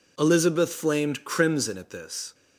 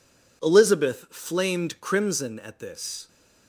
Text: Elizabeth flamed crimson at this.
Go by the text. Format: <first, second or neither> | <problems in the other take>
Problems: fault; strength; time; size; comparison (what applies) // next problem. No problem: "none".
neither | none